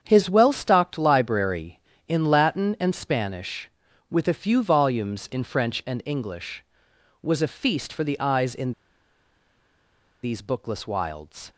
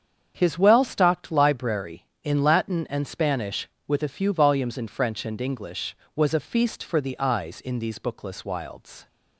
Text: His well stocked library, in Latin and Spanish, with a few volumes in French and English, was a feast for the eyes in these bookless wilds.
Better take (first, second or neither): second